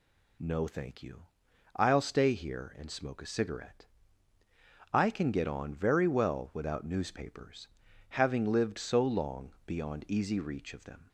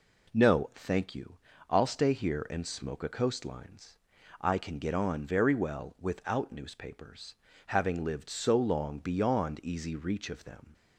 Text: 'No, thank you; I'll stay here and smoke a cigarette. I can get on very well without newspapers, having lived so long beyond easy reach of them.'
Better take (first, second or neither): first